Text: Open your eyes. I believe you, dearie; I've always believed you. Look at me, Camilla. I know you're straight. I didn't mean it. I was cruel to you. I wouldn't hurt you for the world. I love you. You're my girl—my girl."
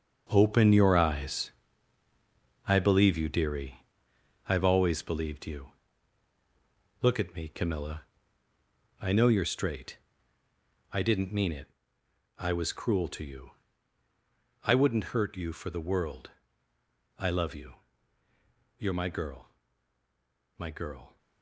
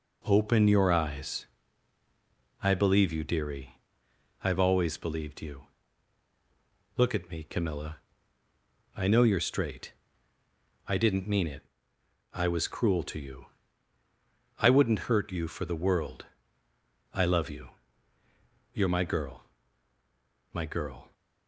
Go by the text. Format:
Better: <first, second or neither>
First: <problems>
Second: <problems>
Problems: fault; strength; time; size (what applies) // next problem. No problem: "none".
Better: second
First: gets quieter; strong; throughout; 10.5 dB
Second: none